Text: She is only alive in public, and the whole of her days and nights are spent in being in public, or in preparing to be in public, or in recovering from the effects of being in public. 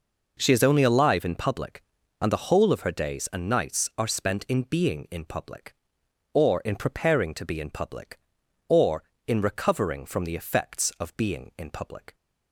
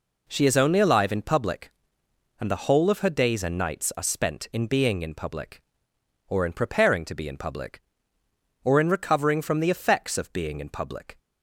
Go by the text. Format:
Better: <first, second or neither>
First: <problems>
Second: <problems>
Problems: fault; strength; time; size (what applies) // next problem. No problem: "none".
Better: neither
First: none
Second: none